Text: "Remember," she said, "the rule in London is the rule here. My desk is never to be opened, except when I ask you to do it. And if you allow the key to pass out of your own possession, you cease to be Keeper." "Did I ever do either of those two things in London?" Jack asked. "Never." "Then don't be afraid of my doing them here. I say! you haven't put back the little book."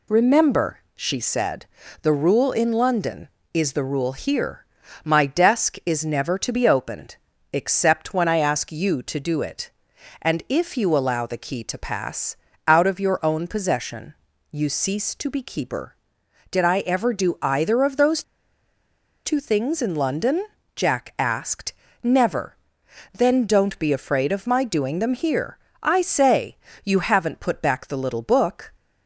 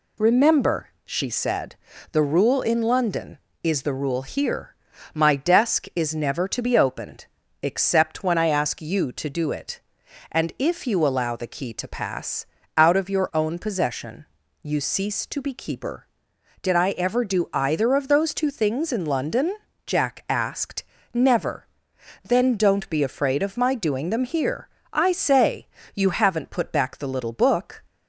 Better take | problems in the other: second | pauses between "pass" and "out"; slight; at 12.3 s; 0.32 s long; slight in the second // pauses between "those" and "two"; at 18.2 s; 1.0 s long

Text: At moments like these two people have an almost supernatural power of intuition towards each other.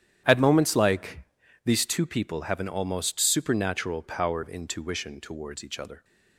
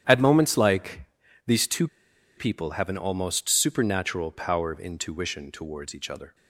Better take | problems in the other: first | starts louder than the rest; strong; until 1.5 s; 10 dB; strong in the first // pauses between "like" and "these"; at 1.0 s; 0.42 s long; also in the first // pauses between "two" and "people"; noticeable; at 1.8 s; 0.49 s long

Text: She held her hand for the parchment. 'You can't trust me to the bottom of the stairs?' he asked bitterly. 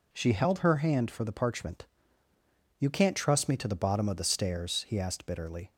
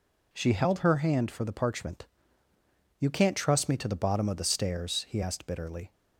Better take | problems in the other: neither | none

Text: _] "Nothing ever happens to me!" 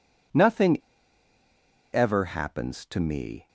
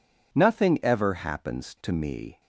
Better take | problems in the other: second | pauses between "Nothing" and "ever"; at 0.7 s; 1.1 s long

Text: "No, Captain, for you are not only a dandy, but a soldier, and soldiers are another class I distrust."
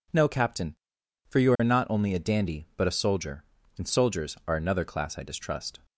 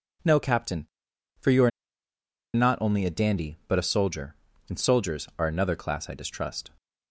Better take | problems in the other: first | pauses between "are" and "not"; noticeable; at 1.7 s; 0.84 s long

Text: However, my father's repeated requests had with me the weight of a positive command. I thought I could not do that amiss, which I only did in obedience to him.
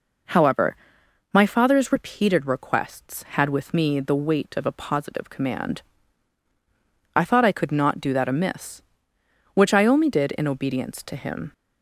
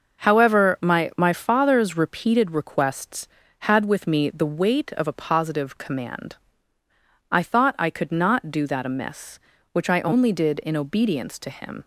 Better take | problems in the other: first | starts louder than the rest; noticeable; until 1.3 s; 6 dB // says "my" twice; at 1.1 s

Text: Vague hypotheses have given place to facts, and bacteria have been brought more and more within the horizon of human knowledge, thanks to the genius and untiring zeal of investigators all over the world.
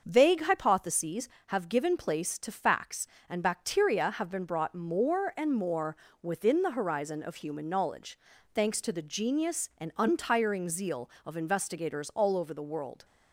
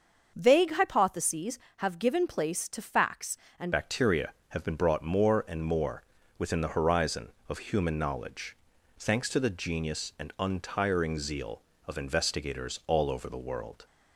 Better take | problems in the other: first | starts louder than the rest; until 1.3 s; 6.5 dB; also in the first // changes voice at "bacteria"; from 3.7 s on; 10.1 s long // pauses between "more" and "within"; slight; at 6.0 s; 0.36 s long; slight in the first

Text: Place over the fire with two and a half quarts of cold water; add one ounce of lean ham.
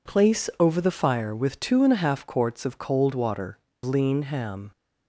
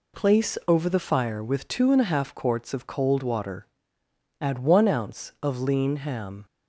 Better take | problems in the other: second | skips "add one ounce of"; at 3.7 s

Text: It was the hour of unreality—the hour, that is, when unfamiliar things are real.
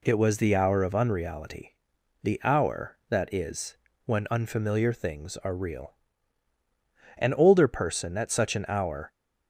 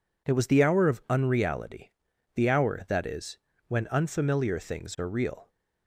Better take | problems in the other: second | goes on to say "An older person at such an hour"; strong; from 7.1 s on; 1.9 s long

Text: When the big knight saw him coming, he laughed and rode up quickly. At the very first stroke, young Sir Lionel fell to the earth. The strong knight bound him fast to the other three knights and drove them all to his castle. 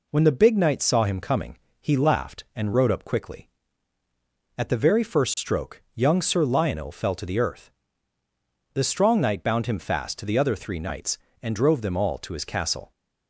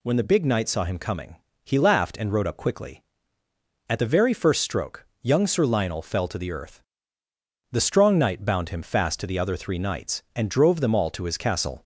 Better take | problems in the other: neither | none

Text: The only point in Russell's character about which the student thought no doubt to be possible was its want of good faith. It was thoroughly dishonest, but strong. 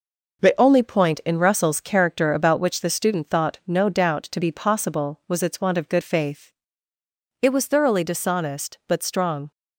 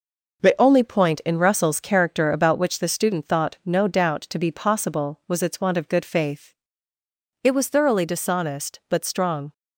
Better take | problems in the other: neither | none

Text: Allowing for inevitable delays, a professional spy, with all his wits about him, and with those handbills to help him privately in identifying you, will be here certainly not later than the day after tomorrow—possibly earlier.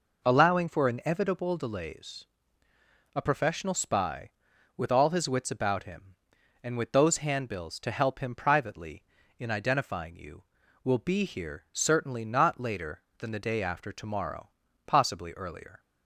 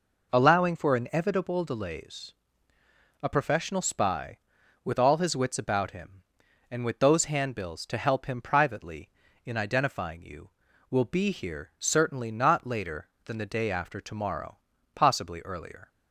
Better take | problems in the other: neither | none

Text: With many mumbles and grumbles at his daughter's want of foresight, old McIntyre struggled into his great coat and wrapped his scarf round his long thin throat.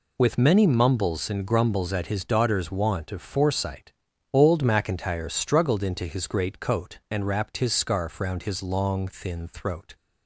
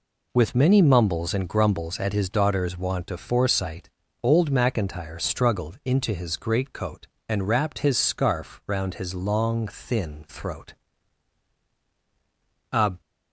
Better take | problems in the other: first | goes on to say "A"; slight; from 12.7 s on; 0.30 s long

